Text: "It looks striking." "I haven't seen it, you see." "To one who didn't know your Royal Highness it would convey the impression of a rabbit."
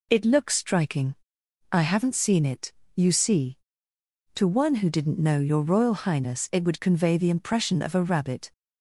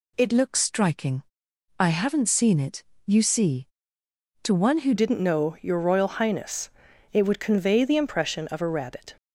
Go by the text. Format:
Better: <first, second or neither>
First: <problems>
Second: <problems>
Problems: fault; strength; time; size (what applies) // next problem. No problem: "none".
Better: first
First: none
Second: changes voice at "didn't"; from 4.9 s on; 4.2 s long // pauses between "Highness" and "it"; at 6.6 s; 0.44 s long